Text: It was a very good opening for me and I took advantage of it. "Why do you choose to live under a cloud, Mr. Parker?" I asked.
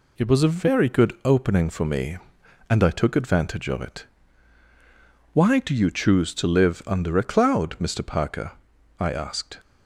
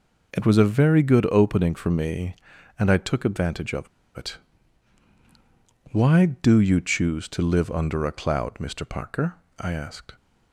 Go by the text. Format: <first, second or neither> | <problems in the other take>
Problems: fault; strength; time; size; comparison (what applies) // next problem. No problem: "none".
first | pauses between "of" and "it"; slight; at 3.8 s; 0.30 s long